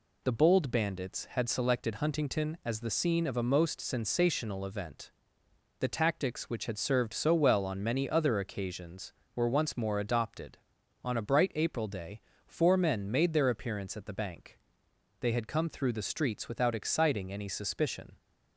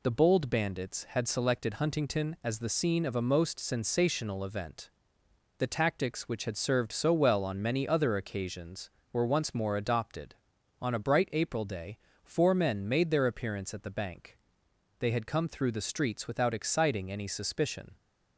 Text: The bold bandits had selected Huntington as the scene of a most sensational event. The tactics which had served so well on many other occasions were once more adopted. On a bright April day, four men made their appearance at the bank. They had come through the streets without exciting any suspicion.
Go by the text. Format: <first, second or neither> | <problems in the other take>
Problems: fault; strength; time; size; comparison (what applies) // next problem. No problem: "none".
neither | none